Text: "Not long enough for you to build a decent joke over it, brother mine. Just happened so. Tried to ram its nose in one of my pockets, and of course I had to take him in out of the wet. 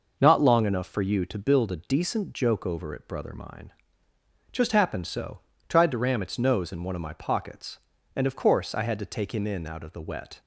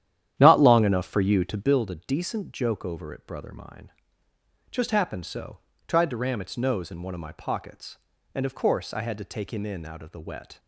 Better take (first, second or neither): first